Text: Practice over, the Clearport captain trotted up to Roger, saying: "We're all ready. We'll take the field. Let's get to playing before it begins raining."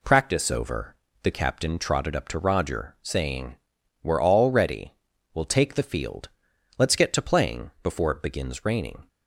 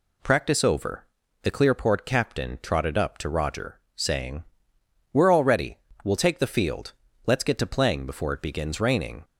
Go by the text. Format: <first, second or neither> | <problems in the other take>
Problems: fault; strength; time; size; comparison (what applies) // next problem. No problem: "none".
second | skips "Clearport"; at 1.3 s